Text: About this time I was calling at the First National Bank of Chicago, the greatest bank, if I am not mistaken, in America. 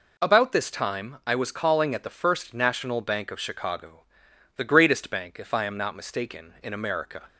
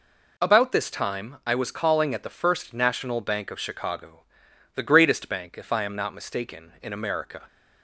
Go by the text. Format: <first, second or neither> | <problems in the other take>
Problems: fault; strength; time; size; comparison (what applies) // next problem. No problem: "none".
neither | none